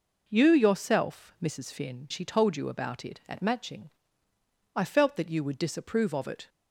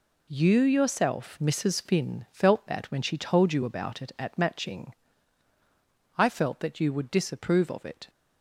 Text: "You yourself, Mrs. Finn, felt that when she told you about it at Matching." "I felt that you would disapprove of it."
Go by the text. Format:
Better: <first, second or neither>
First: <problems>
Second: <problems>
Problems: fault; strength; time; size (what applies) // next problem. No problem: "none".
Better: second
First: skips "felt that when"; at 2.0 s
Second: none